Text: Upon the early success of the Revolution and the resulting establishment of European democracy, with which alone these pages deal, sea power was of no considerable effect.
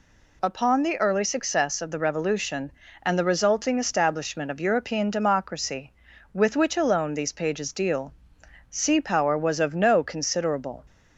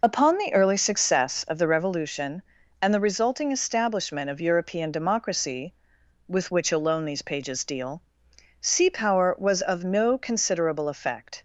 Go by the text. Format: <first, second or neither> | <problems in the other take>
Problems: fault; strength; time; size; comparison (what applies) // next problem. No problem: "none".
second | stops before "effect"; at 10.8 s